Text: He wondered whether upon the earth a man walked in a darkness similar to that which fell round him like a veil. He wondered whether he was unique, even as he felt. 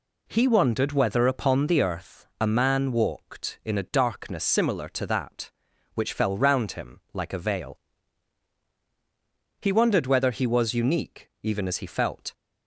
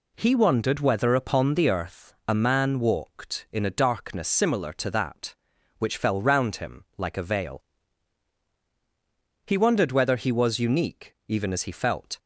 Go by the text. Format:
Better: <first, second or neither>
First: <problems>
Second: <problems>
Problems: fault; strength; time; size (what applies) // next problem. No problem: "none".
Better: neither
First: none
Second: none